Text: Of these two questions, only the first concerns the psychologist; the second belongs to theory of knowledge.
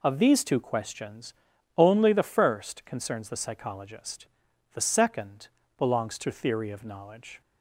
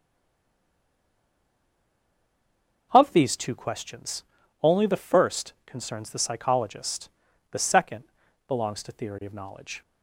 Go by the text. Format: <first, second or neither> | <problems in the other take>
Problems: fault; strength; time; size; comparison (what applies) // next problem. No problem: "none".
first | stays silent before the first word; strong; until 2.9 s; 2.9 s long // pauses between "second" and "belongs"; at 8.0 s; 0.42 s long; slight in the first